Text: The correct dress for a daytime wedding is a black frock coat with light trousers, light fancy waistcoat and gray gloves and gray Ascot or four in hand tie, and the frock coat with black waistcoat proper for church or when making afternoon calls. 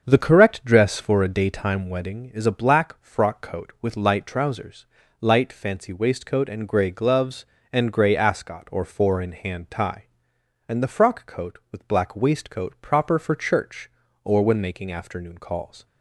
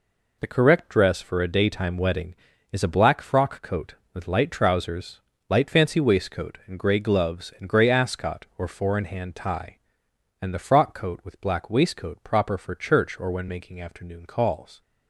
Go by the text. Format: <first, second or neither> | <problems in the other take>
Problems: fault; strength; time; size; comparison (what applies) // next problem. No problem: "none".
second | starts louder than the rest; until 1.2 s; 7 dB